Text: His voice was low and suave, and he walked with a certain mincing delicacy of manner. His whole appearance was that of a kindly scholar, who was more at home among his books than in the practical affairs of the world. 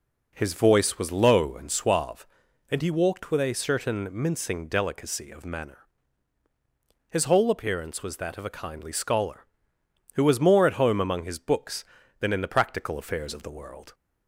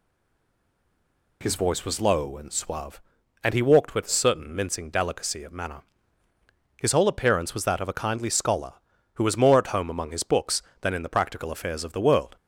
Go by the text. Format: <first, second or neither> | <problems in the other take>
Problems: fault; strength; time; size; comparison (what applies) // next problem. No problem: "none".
first | stays silent before the first word; noticeable; until 1.4 s; 1.4 s long